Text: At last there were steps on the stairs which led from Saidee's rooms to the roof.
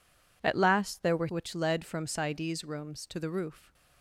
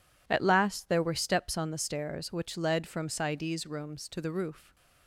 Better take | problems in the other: second | skips "steps on the stairs"; at 1.2 s

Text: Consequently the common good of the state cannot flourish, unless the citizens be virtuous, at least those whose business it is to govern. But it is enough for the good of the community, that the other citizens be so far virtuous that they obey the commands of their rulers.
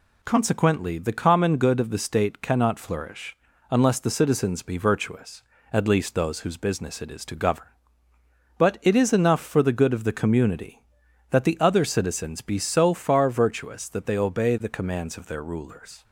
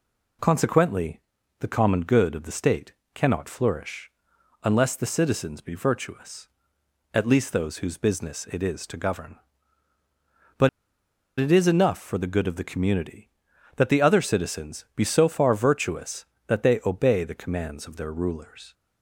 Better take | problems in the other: first | pauses between "Consequently" and "the"; at 1.1 s; 0.40 s long // pauses between "state" and "cannot"; slight; at 2.9 s; 0.20 s long // pauses between "But" and "it"; noticeable; at 10.6 s; 0.70 s long

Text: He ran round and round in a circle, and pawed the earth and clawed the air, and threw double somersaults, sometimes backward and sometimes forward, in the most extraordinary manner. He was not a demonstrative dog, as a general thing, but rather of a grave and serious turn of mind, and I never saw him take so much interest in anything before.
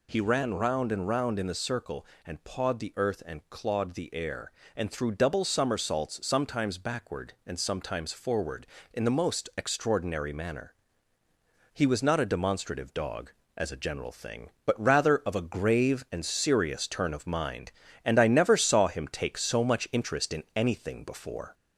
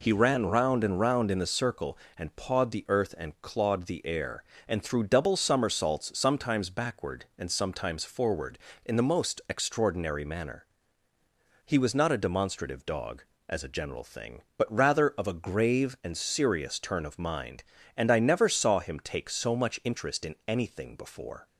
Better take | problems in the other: second | gets louder; slight; throughout; 2 dB

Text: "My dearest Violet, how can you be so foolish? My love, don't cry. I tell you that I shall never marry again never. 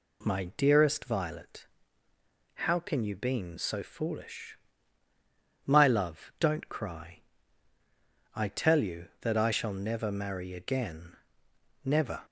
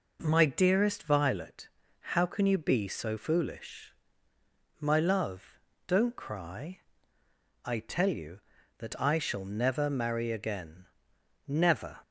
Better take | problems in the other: second | says "been" for "be"; at 3.1 s // pauses between "again" and "never"; noticeable; at 11.1 s; 0.70 s long; noticeable in the second

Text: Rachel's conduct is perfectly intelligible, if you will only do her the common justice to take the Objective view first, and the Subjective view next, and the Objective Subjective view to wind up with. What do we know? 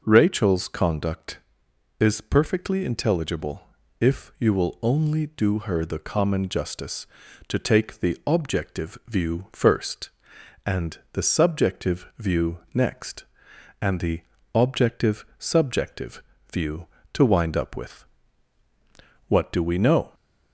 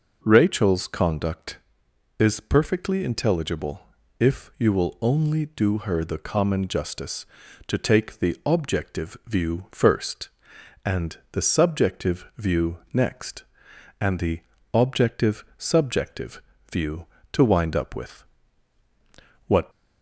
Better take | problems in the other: first | pauses between "view" and "next"; slight; at 12.7 s; 0.16 s long; slight in the first // pauses between "the" and "Objective"; slight; at 14.4 s; 0.34 s long; slight in the first // pauses between "Subjective" and "view"; slight; at 16.3 s; 0.32 s long; slight in the first // stops before "do we know"; at 19.7 s

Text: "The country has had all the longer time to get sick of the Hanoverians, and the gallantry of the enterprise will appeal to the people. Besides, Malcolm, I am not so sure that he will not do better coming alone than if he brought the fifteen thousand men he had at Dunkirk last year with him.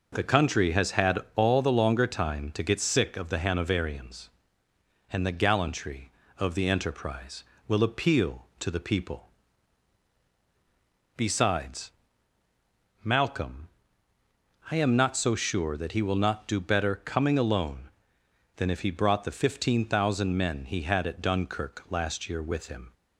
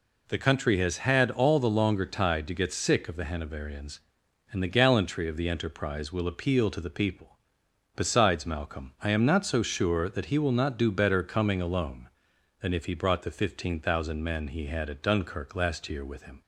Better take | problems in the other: first | says "tide" for "time"; at 2.0 s

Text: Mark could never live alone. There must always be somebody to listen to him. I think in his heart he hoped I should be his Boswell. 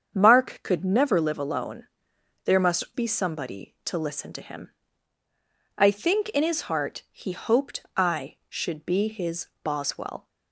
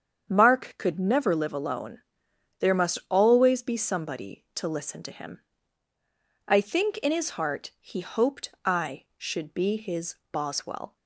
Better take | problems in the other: second | starts louder than the rest; strong; until 1.1 s; 7.5 dB; strong in the second // skips "always"; at 2.8 s // pauses between "his" and "Boswell"; slight; at 9.4 s; 0.16 s long; slight in the second

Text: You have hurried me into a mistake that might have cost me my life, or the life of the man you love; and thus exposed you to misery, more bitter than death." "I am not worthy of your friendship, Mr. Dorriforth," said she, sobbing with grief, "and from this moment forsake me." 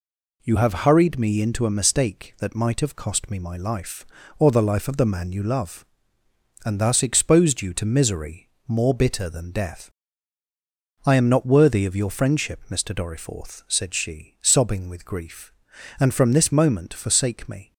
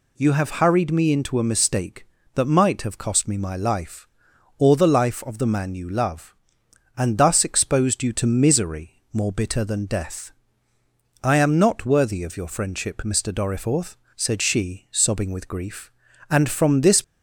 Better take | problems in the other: first | stops before "moment forsake me"; at 17.0 s

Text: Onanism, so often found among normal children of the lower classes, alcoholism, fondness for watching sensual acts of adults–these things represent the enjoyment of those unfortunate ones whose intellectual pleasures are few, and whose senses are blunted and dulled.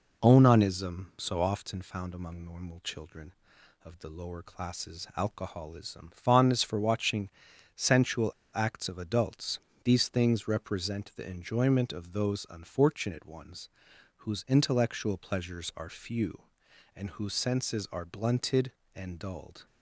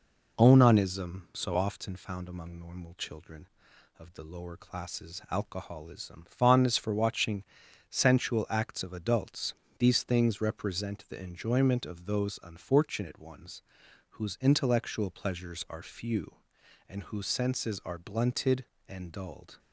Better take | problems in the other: second | pauses between "watching" and "sensual"; at 7.2 s; 0.44 s long; also in the second // pauses between "sensual" and "acts"; slight; at 8.2 s; 0.25 s long // pauses between "ones" and "whose"; noticeable; at 13.6 s; 0.48 s long; noticeable in the second

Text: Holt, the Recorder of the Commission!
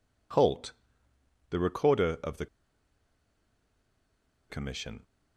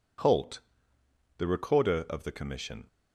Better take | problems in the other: second | pauses between "the" and "Commission"; strong; at 2.4 s; 2.0 s long

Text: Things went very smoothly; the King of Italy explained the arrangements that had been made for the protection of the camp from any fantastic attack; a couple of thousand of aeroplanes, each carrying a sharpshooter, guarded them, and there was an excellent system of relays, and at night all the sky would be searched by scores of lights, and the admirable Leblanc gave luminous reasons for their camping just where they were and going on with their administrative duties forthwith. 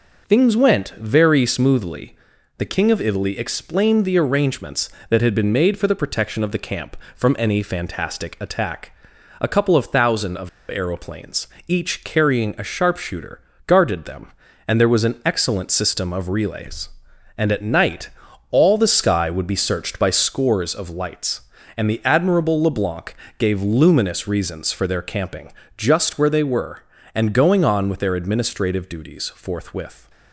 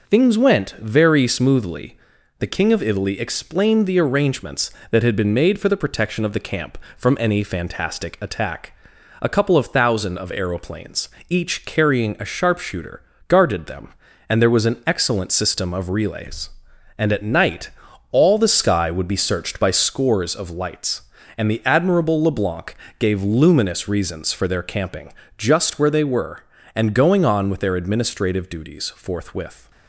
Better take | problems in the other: second | pauses between "of" and "aeroplanes"; slight; at 10.4 s; 0.20 s long // pauses between "night" and "all"; at 18.0 s; 0.42 s long; also in the second // pauses between "Leblanc" and "gave"; slight; at 23.1 s; 0.24 s long; slight in the second // pauses between "camping" and "just"; slight; at 25.5 s; 0.24 s long; slight in the second

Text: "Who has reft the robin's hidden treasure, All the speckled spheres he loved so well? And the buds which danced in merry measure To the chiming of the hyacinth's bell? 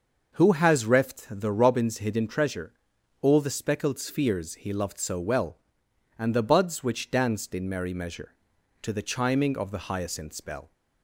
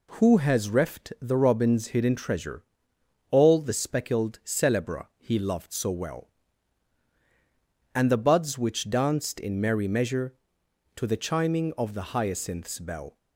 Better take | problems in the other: first | says "celebra" for "spheres"; at 4.4 s

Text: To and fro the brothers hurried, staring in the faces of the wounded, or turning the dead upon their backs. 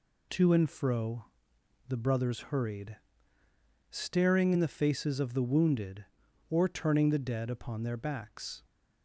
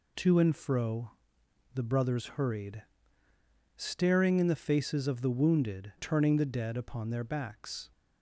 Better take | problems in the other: first | pauses between "fro" and "the"; noticeable; at 1.1 s; 0.62 s long; noticeable in the first // skips "or"; at 5.9 s

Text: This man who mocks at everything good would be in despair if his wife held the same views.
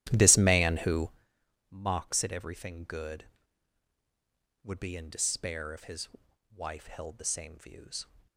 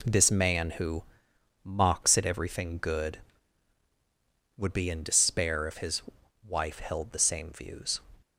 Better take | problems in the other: second | starts louder than the rest; strong; until 1.2 s; 12.5 dB // pauses between "who" and "mocks"; noticeable; at 1.0 s; 0.60 s long; noticeable in the second // pauses between "his" and "wife"; noticeable; at 6.0 s; 0.48 s long; noticeable in the second

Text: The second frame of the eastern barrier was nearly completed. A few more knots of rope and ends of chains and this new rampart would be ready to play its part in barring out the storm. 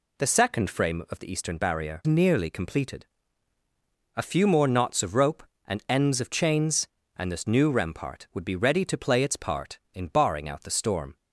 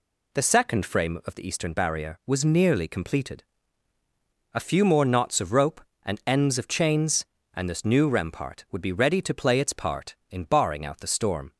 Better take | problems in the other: second | skips "was"; at 2.0 s

